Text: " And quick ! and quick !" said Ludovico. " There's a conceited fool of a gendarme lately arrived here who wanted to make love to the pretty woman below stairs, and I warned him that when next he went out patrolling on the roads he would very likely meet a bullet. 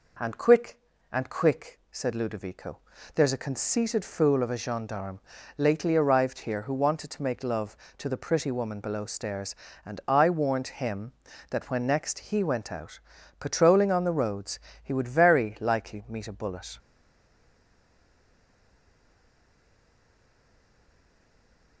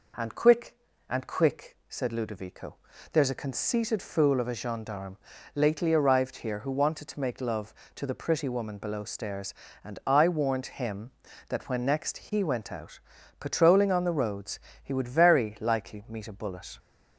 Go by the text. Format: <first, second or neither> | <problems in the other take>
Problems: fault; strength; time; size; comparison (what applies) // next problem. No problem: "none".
second | pauses between "gendarme" and "lately"; at 5.1 s; 0.40 s long; also in the second // pauses between "out" and "patrolling"; at 12.9 s; 0.42 s long; also in the second // pauses between "roads" and "he"; slight; at 14.5 s; 0.24 s long; slight in the second // stays silent after the last word; strong; from 16.7 s on; 5.1 s long